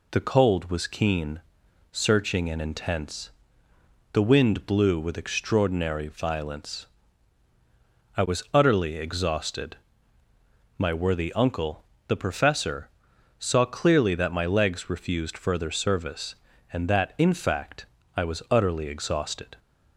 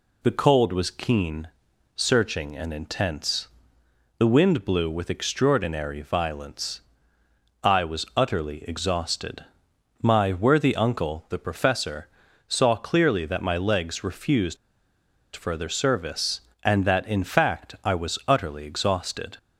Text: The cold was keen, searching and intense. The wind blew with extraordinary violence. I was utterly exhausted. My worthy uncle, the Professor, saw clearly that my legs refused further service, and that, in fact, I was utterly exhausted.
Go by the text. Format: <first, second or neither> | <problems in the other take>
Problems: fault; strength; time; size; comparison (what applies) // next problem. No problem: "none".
first | pauses between "refused" and "further"; noticeable; at 14.5 s; 0.78 s long